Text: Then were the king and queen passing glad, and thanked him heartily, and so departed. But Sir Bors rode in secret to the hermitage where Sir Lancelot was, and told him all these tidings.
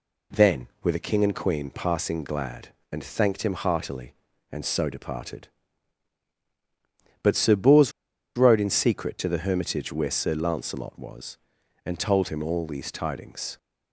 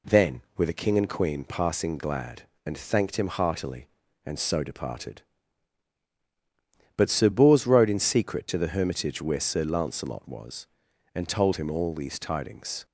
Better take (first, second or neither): second